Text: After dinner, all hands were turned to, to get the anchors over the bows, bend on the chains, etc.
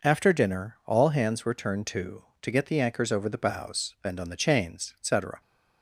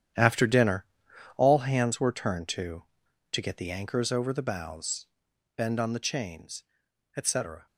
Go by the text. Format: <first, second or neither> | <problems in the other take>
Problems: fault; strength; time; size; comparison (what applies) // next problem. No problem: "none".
first | gets quieter; strong; throughout; 12 dB